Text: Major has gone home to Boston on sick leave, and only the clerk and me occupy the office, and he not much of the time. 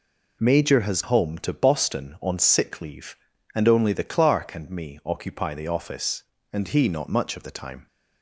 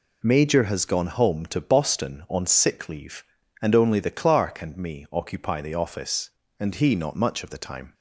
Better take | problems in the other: second | skips "gone"; at 1.0 s

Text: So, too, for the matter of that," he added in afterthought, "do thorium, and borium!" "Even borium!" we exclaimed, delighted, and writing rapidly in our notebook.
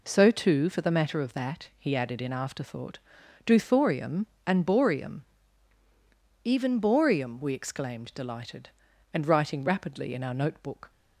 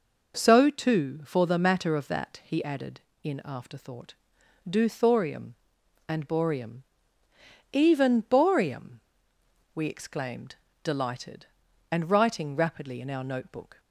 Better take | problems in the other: neither | none

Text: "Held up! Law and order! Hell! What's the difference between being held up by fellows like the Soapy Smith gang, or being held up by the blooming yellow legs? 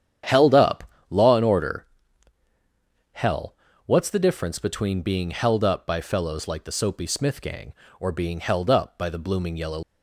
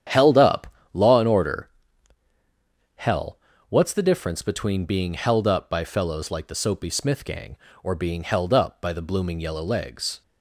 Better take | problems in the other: second | starts louder than the rest; strong; until 1.5 s; 9.5 dB; strong in the second // stops before "legs"; at 9.8 s

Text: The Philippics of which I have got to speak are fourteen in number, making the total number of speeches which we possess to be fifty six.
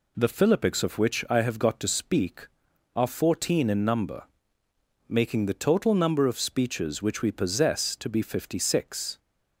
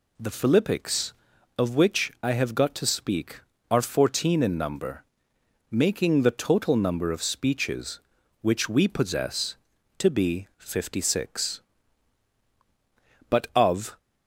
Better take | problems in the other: first | pauses between "be" and "fifty"; slight; at 10.4 s; 0.22 s long // goes on to say "But of"; noticeable; from 13.2 s on; 0.68 s long

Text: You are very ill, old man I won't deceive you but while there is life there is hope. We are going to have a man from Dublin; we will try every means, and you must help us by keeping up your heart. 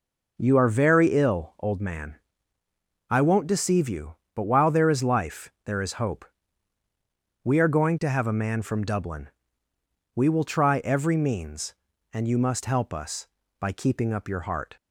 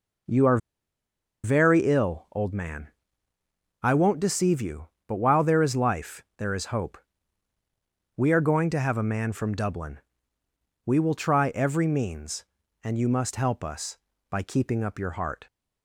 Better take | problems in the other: first | pauses between "are" and "very"; noticeable; at 0.5 s; 0.86 s long // pauses between "man" and "I"; noticeable; at 2.8 s; 0.96 s long; noticeable in the first

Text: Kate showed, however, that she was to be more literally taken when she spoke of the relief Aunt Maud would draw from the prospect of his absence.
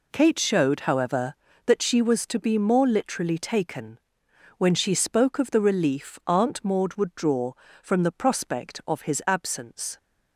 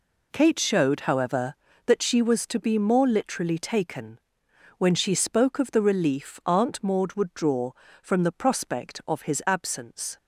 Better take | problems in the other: neither | pauses between "taken" and "when"; noticeable; the same in both

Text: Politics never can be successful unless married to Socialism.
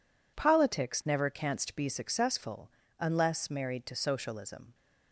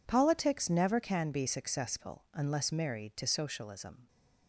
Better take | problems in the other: second | says "canst" for "can"; at 1.3 s // pauses between "successful" and "unless"; slight; at 2.6 s; 0.30 s long

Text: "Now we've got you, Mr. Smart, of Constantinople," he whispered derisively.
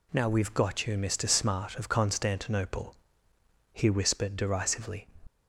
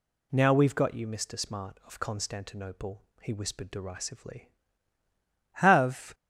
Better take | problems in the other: first | goes on to say "Have"; from 5.5 s on; 0.60 s long

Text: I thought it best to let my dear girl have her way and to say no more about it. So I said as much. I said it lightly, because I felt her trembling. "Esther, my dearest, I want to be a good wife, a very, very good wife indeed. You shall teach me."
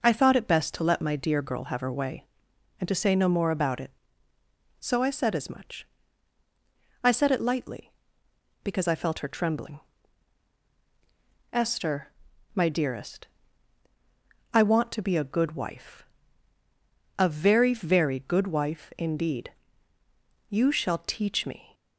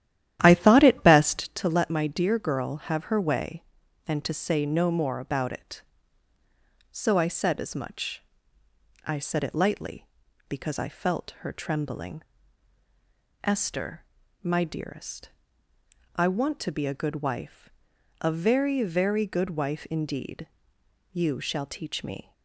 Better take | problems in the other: first | starts louder than the rest; strong; until 1.6 s; 11.5 dB

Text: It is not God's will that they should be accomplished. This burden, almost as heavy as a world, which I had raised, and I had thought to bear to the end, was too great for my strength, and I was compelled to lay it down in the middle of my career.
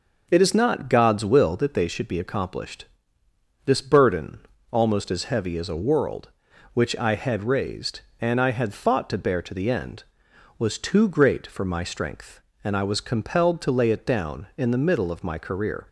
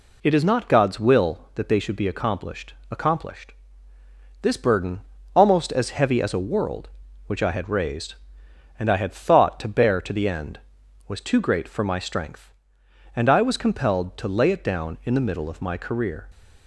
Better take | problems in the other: first | says "accomplished" twice; at 2.8 s

